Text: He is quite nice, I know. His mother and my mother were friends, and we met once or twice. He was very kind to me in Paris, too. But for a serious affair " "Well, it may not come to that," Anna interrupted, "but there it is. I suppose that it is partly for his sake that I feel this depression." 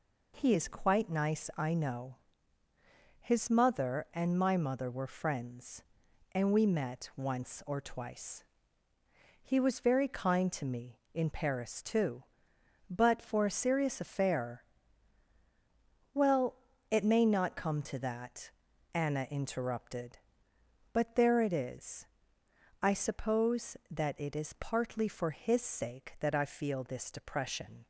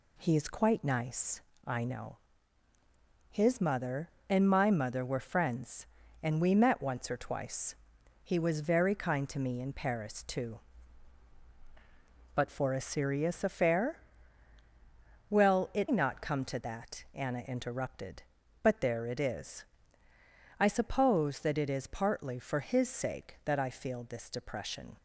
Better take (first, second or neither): first